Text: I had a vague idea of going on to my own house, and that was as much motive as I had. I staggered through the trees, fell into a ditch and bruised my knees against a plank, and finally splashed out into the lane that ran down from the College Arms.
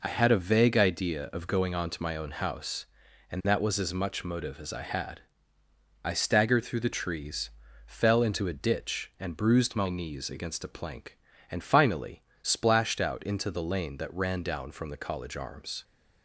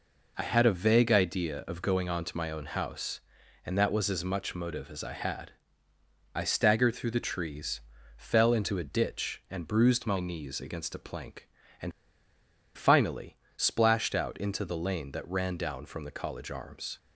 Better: first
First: pauses between "finally" and "splashed"; slight; at 12.2 s; 0.18 s long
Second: pauses between "and" and "finally"; noticeable; at 11.9 s; 0.85 s long // pauses between "finally" and "splashed"; slight; at 13.3 s; 0.18 s long

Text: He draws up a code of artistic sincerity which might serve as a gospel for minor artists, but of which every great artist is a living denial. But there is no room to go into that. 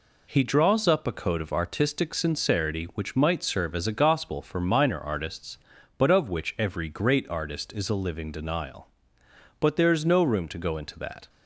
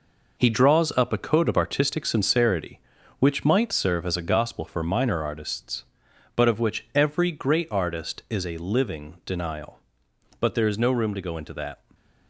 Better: first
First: none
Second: gets quieter; strong; throughout; 7.5 dB

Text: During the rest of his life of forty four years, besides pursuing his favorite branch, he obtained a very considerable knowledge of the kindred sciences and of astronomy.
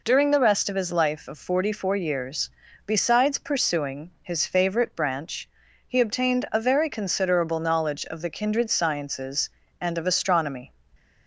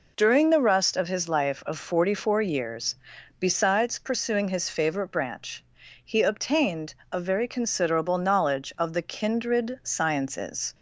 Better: first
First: none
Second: pauses between "obtained" and "a"; slight; at 6.9 s; 0.16 s long // stops before "and of astronomy"; at 10.7 s

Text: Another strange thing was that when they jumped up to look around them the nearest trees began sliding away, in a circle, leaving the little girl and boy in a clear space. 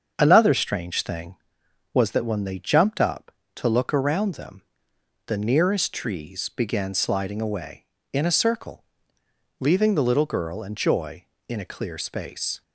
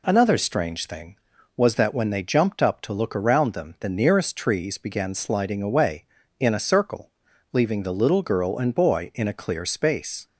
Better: second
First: starts louder than the rest; until 1.1 s; 7 dB // pauses between "them" and "the"; noticeable; at 4.6 s; 0.64 s long // says "joy" for "boy"; at 10.7 s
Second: none

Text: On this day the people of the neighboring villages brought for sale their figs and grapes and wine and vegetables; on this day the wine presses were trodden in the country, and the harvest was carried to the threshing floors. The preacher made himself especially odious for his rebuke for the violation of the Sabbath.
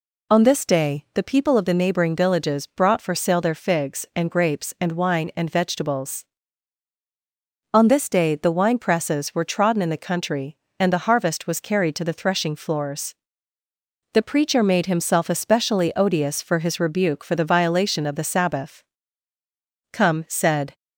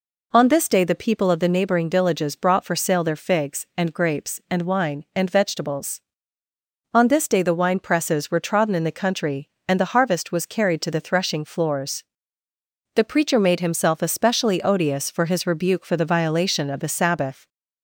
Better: second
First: goes on to say "Come said"; noticeable; from 19.9 s on; 0.84 s long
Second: none

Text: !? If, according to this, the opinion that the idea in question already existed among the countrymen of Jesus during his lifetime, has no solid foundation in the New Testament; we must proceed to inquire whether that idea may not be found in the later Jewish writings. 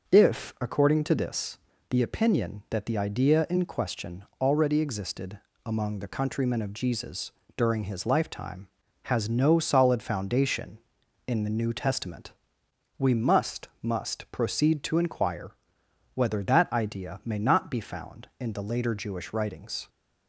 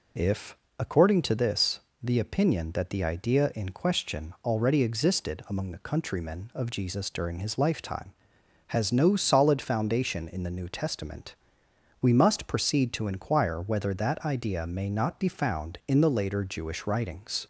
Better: second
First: pauses between "question" and "already"; slight; at 4.2 s; 0.18 s long // pauses between "existed" and "among"; slight; at 5.3 s; 0.26 s long // pauses between "Jesus" and "during"; slight; at 7.3 s; 0.24 s long // says "must" twice; at 13.8 s // pauses between "inquire" and "whether"; noticeable; at 15.5 s; 0.64 s long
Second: none

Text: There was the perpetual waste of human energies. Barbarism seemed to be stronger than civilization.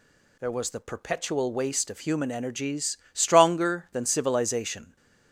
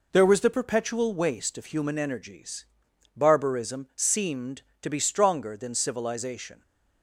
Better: second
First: skips "Barbarism seemed to be"; at 3.0 s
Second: none

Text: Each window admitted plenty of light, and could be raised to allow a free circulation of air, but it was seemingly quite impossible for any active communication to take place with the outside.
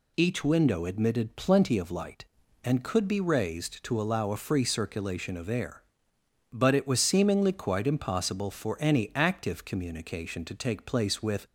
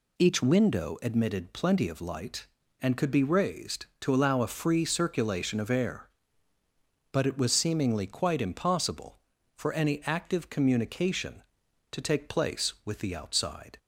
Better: second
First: stops before "the outside"; at 11.4 s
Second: none

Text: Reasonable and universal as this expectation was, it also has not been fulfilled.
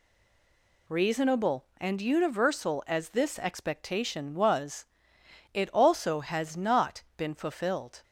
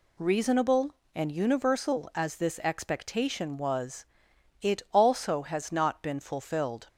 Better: second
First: stays silent before the first word; slight; until 0.8 s; 0.8 s long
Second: none

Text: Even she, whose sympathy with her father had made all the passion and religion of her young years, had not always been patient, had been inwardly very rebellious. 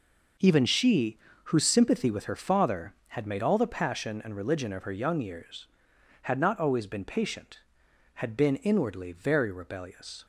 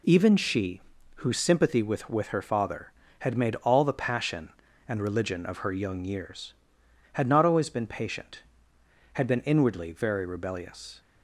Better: first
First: none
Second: says "with" twice; at 2.1 s

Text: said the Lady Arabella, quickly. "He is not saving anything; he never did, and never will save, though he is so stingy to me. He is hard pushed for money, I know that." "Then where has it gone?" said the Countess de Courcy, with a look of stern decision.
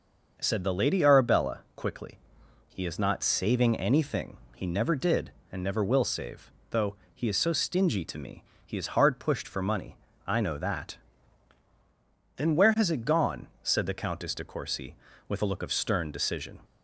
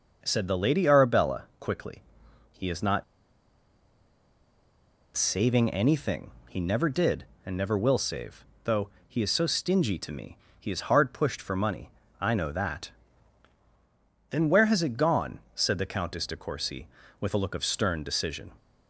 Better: first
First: starts louder than the rest; noticeable; until 1.4 s; 6 dB // pauses between "though" and "he"; slight; at 6.9 s; 0.20 s long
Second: starts louder than the rest; noticeable; until 1.2 s; 6 dB // pauses between "not" and "saving"; strong; at 3.0 s; 2.1 s long // pauses between "though" and "he"; slight; at 8.8 s; 0.20 s long

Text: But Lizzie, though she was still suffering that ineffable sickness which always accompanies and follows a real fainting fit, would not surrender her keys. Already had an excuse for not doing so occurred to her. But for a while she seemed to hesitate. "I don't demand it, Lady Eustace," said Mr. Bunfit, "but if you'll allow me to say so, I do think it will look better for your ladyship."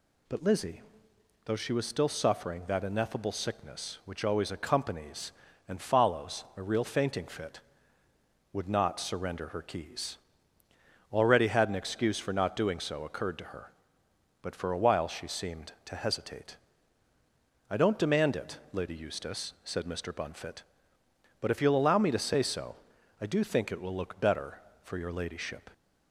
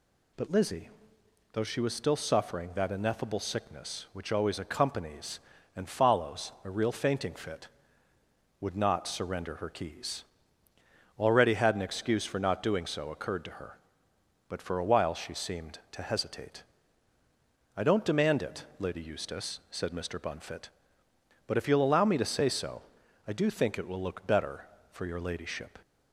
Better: neither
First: none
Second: none

